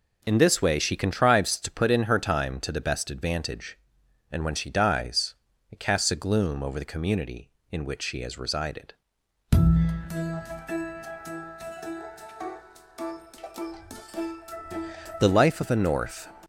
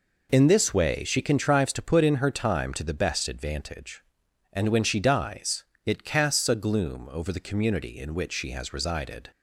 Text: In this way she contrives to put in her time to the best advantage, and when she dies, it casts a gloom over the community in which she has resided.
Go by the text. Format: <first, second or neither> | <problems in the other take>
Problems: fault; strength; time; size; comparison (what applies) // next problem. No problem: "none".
second | goes on to say "The life of a North"; strong; from 9.5 s on; 6.7 s long